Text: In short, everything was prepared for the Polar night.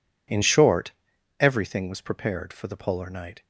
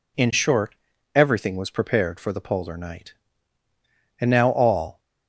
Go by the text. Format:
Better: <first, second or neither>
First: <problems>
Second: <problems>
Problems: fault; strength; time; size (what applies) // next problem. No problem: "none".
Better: first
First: none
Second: goes on to say "And now all"; noticeable; from 4.1 s on; 0.80 s long